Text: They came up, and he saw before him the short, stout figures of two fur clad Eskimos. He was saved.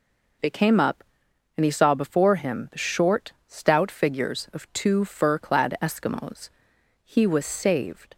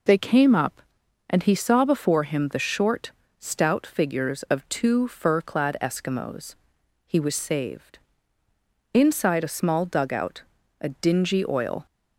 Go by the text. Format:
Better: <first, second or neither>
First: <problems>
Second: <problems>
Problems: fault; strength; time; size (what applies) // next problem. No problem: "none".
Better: first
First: none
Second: goes on to say "Inside a small dugout a dingy oil"; strong; from 8.9 s on; 2.9 s long